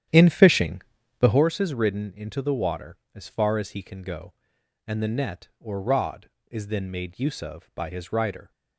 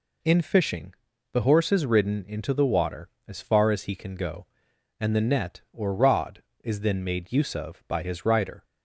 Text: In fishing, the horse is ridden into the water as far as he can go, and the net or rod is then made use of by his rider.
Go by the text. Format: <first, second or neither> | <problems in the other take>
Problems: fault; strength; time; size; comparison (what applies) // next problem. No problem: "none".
second | starts louder than the rest; strong; until 1.4 s; 10.5 dB